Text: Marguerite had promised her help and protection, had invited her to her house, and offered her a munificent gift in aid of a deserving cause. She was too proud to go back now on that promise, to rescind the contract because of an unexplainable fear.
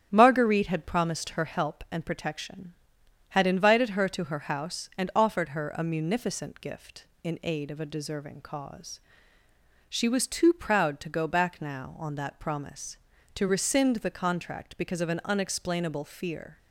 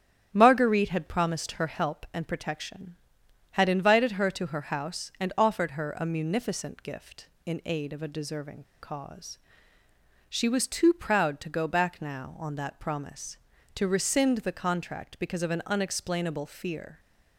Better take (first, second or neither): first